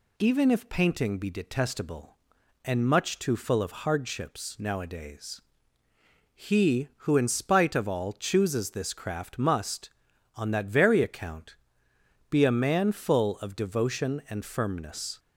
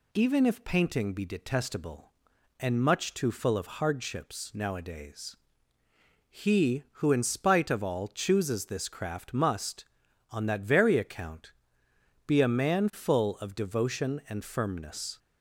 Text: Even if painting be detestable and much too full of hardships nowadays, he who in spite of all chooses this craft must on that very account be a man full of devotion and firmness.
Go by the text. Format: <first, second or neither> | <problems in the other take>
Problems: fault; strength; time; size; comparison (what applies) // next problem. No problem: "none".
neither | pauses between "account" and "be"; noticeable; the same in both